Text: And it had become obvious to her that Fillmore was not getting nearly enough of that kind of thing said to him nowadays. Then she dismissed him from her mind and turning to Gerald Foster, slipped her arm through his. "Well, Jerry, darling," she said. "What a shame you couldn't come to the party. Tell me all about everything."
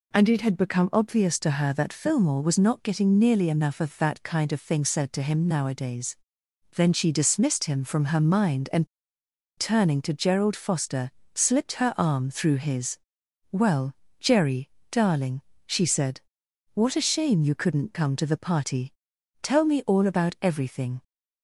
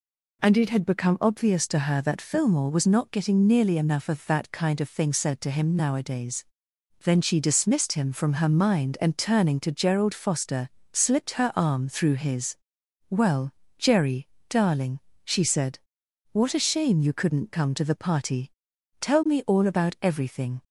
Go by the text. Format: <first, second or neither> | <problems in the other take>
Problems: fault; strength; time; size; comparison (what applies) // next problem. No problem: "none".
second | pauses between "and" and "turning"; noticeable; at 8.8 s; 0.71 s long